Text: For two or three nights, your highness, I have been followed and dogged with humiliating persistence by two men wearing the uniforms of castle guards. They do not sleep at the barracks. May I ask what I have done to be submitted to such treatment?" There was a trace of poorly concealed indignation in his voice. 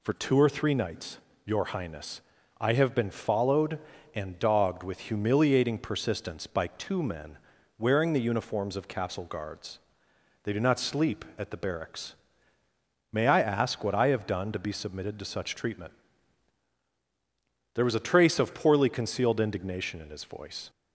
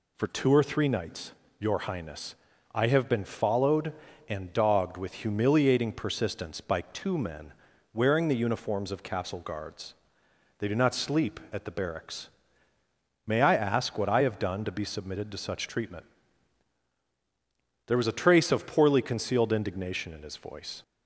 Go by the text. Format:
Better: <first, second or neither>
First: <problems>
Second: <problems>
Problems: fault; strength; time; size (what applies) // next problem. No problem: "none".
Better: neither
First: pauses between "men" and "wearing"; at 7.3 s; 0.40 s long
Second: pauses between "men" and "wearing"; at 7.5 s; 0.40 s long